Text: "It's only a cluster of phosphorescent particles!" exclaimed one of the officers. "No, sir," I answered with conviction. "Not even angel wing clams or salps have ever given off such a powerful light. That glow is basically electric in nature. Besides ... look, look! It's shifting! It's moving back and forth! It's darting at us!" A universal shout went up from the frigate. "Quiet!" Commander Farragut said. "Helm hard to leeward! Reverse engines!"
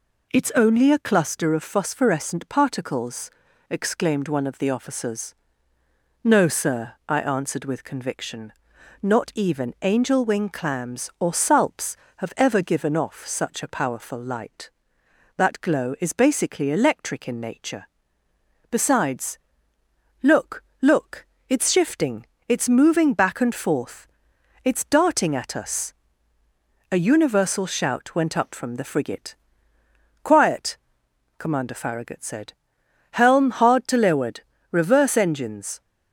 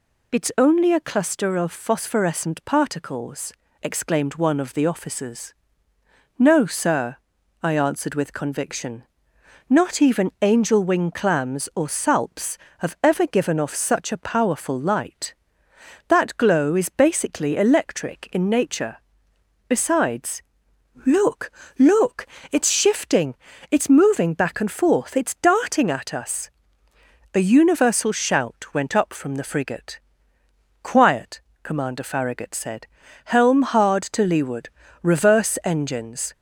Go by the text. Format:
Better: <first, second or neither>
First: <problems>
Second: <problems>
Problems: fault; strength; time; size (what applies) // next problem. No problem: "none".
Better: neither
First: none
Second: none